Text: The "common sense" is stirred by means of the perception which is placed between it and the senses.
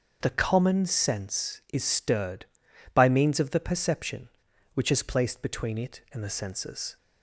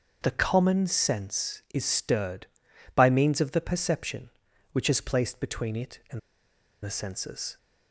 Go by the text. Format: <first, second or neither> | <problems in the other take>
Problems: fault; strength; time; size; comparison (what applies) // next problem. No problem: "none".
first | starts louder than the rest; until 1.2 s; 6.5 dB; also in the first // pauses between "and" and "the"; noticeable; at 6.1 s; 0.65 s long